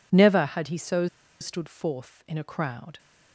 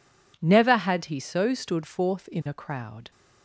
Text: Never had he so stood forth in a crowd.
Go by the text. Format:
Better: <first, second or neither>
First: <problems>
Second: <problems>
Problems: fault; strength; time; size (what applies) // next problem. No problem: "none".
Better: second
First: pauses between "so" and "stood"; slight; at 1.0 s; 0.34 s long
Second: none